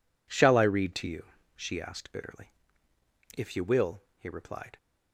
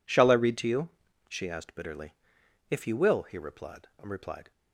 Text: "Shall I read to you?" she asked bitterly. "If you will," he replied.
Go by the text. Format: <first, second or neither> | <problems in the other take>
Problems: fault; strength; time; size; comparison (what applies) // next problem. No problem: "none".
first | says "replied" twice; at 4.0 s